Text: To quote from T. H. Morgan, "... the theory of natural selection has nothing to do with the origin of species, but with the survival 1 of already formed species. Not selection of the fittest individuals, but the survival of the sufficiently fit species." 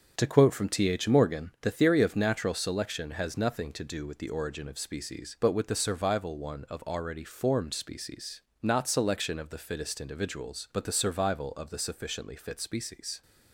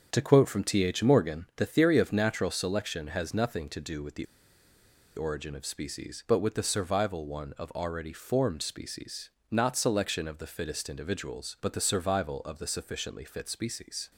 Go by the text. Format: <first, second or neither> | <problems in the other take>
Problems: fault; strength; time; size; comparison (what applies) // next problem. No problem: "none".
first | starts louder than the rest; strong; until 1.1 s; 7 dB; strong in the first // pauses between "the" and "origin"; noticeable; at 4.2 s; 0.90 s long